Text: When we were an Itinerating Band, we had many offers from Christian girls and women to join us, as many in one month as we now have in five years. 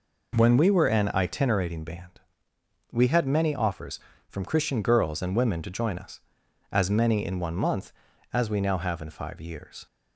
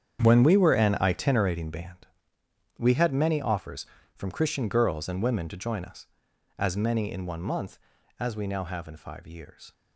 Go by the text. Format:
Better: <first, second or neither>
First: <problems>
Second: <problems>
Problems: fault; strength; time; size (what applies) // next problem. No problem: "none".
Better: first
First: none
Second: gets quieter; strong; throughout; 13.5 dB